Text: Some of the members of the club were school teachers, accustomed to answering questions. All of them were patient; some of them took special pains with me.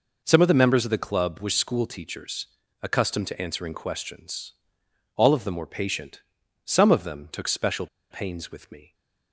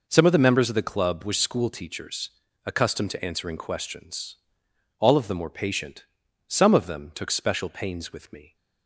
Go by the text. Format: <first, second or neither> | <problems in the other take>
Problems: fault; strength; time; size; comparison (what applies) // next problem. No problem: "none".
second | pauses between "special" and "pains"; slight; at 7.8 s; 0.24 s long